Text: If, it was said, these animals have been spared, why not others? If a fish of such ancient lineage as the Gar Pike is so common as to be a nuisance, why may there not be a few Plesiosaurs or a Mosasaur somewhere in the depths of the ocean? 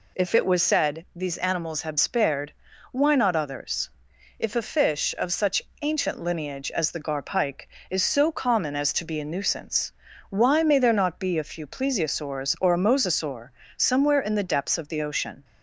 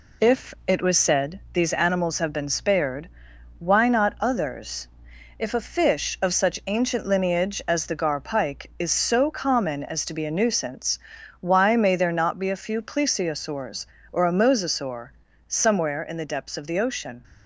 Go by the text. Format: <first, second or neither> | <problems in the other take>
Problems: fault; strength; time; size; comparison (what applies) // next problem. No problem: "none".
second | skips "been"; at 1.9 s // pauses between "such" and "ancient"; slight; at 5.6 s; 0.22 s long // pauses between "Mosasaur" and "somewhere"; slight; at 13.5 s; 0.26 s long; slight in the second